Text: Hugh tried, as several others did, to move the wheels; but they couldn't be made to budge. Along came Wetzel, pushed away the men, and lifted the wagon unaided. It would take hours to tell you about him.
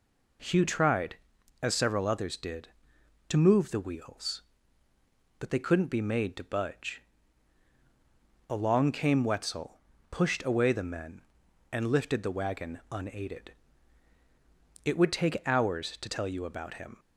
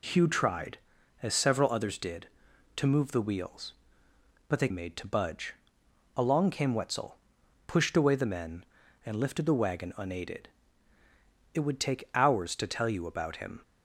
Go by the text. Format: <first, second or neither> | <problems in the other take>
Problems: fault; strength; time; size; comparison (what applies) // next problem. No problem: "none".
first | skips "couldn't be"; at 4.6 s